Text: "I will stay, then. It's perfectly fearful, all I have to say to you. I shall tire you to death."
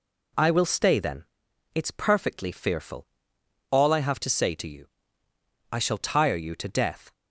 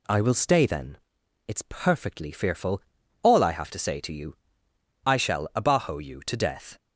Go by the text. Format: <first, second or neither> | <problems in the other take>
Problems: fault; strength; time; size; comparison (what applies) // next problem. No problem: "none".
first | says "abajo" for "tire"; at 5.5 s